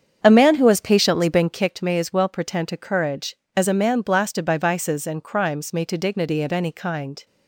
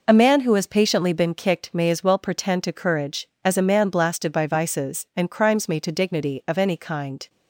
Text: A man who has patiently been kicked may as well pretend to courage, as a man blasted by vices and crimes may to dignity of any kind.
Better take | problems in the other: second | starts louder than the rest; strong; until 1.7 s; 7.5 dB

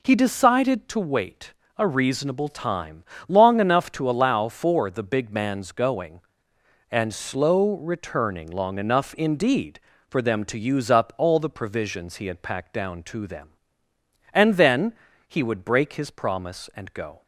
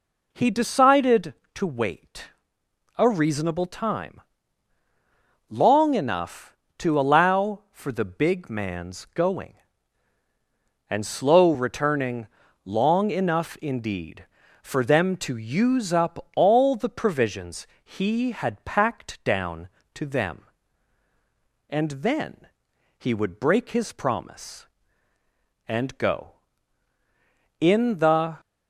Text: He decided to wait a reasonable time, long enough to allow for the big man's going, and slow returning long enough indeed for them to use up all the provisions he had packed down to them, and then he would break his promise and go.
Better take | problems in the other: first | pauses between "wait" and "a"; noticeable; at 2.2 s; 0.68 s long; slight in the first // pauses between "returning" and "long"; at 12.2 s; 0.38 s long // pauses between "provisions" and "he"; slight; at 17.6 s; 0.18 s long // pauses between "then" and "he"; noticeable; at 22.4 s; 0.52 s long; slight in the first // goes on to say "In the"; noticeable; from 27.5 s on; 0.80 s long

